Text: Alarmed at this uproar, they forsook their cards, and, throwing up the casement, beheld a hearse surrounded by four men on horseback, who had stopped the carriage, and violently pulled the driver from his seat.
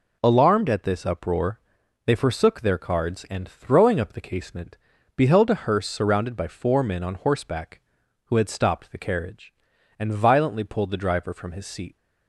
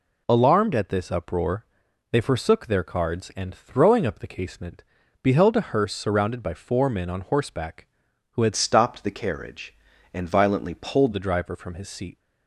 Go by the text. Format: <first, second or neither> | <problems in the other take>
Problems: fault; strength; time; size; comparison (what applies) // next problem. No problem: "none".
first | changes voice from "stopped" to "pulled"; from 8.5 to 11.1 s; 2.6 s long